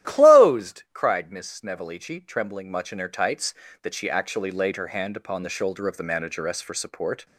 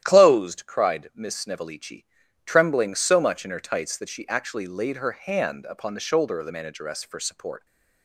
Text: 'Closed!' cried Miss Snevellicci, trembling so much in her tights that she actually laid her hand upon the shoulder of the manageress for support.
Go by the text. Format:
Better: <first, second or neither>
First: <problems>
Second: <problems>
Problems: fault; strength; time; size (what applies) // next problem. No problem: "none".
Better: second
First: starts louder than the rest; strong; until 1.1 s; 12 dB // skips "so"; at 2.6 s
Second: starts louder than the rest; strong; until 1.0 s; 11 dB